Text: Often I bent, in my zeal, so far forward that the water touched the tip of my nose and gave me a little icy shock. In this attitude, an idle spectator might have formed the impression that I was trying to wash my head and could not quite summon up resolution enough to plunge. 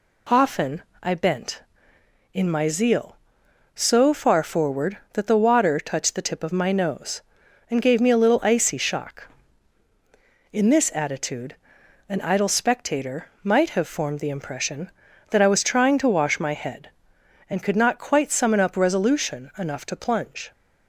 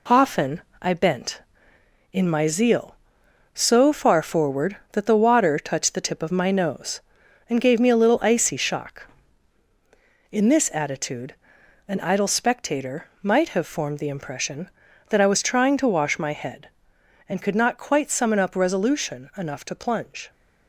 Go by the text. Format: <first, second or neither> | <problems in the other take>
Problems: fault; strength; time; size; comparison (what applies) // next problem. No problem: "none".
first | gets quieter; noticeable; throughout; 5.5 dB // pauses between "Often" and "I"; slight; at 0.6 s; 0.20 s long; slight in the first